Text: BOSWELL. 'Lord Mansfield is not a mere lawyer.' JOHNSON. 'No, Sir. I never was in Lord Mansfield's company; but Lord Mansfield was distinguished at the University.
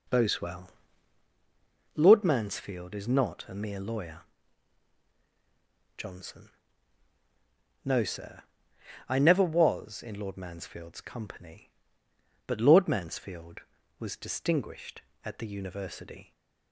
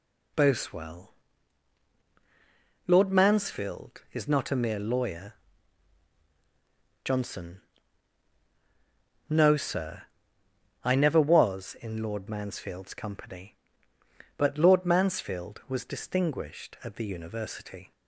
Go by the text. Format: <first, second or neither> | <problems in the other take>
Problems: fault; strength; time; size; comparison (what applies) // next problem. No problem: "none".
second | starts louder than the rest; noticeable; until 1.2 s; 4.5 dB